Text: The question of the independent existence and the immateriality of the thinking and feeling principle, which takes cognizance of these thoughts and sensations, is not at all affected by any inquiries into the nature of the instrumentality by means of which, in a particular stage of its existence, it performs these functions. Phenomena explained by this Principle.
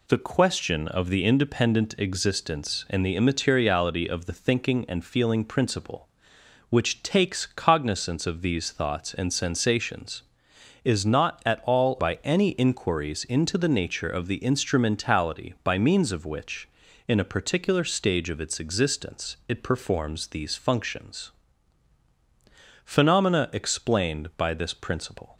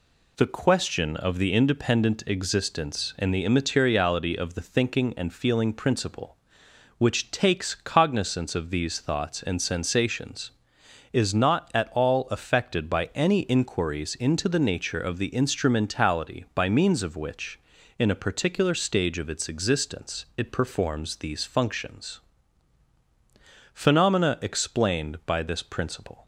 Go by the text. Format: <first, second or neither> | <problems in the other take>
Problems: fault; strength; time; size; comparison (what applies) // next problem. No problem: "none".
second | skips "affected"; at 11.9 s